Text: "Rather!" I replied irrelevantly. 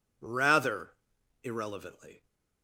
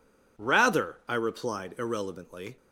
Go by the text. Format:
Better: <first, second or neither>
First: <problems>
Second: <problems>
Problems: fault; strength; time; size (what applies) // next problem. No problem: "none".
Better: second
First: skips "I replied"; at 1.1 s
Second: none